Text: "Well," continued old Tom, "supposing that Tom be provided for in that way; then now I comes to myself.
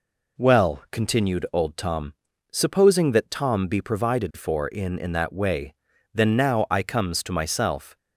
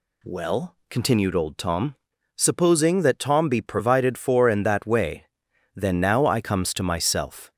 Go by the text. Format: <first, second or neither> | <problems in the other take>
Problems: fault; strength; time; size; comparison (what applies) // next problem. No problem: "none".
second | says "in" twice; at 4.9 s